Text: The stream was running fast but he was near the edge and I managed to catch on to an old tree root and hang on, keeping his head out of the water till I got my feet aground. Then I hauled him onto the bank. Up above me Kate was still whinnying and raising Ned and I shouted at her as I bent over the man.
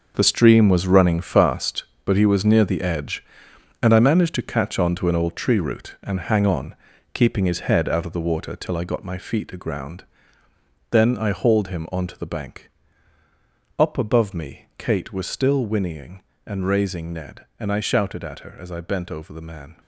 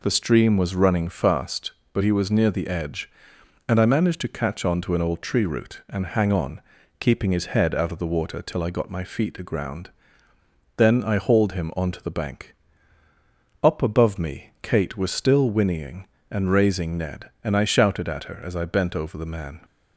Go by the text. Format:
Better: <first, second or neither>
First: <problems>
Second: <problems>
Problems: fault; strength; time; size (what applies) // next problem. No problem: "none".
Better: second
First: gets quieter; strong; throughout; 11.5 dB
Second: none